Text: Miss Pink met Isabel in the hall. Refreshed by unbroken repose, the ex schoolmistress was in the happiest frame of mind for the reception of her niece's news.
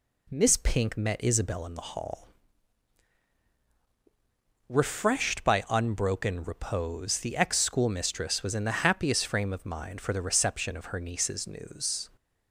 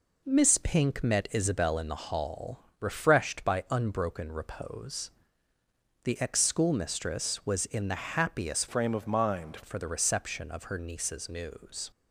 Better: first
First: none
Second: changes voice from "frame" to "mind"; from 8.6 to 9.5 s; 0.9 s long

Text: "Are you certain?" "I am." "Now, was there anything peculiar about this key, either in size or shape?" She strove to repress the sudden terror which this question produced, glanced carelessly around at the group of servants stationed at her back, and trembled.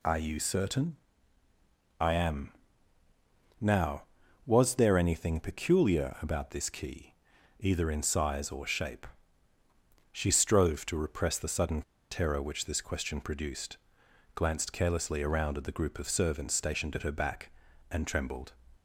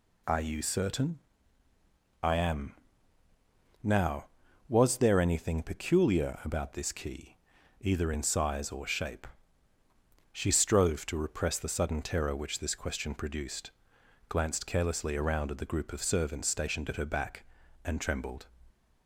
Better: second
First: pauses between "sudden" and "terror"; slight; at 11.8 s; 0.27 s long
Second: none

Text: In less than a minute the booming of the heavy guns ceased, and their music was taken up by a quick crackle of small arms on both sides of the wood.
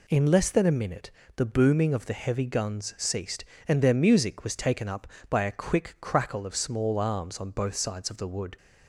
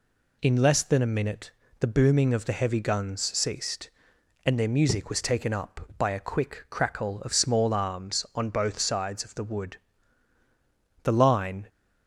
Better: first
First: pauses between "minute" and "the"; slight; at 1.1 s; 0.24 s long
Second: pauses between "minute" and "the"; slight; at 1.5 s; 0.30 s long // pauses between "guns" and "ceased"; slight; at 3.2 s; 0.16 s long // goes on to say "The line"; noticeable; from 11.0 s on; 0.64 s long

